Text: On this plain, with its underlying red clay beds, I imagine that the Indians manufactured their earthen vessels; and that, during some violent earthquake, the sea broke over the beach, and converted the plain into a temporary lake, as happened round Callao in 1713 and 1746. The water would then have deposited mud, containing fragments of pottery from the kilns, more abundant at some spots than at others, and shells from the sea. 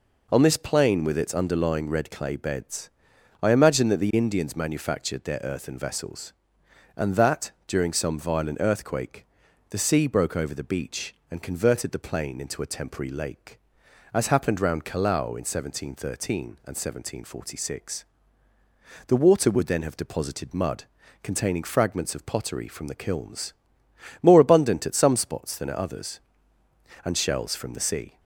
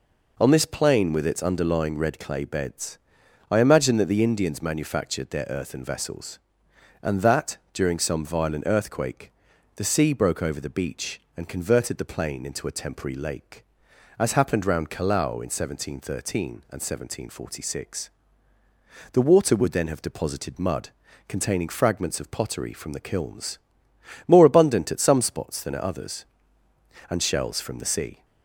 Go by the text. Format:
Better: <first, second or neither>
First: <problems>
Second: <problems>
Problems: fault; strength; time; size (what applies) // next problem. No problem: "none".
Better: neither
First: none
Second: none